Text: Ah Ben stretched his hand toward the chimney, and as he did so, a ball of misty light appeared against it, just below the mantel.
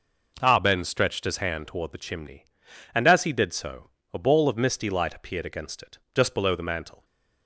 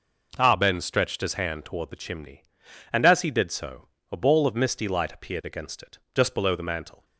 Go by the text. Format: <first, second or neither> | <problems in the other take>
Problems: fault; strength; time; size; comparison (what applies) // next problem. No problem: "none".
neither | none